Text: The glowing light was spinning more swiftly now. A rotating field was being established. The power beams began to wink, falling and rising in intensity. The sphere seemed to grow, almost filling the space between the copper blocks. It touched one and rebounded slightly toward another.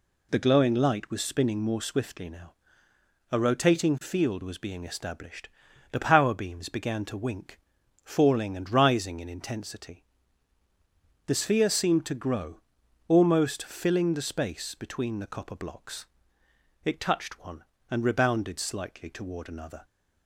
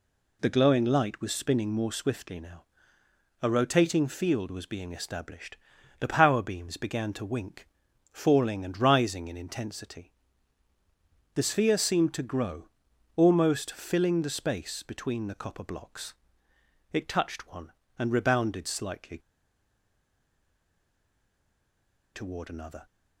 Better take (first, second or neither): first